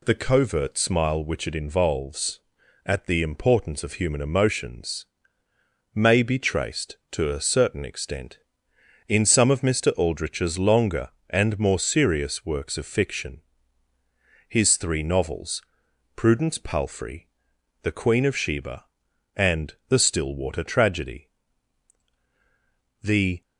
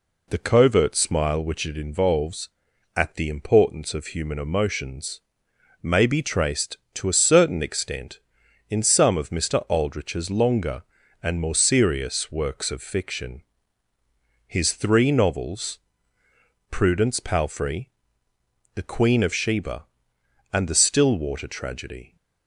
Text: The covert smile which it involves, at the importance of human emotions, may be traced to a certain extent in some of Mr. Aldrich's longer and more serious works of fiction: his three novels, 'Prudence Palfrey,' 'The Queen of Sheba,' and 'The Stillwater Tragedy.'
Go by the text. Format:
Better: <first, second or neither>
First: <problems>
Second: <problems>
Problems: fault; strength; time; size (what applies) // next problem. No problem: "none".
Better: second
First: goes on to say "The"; slight; from 23.0 s on; 0.40 s long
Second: none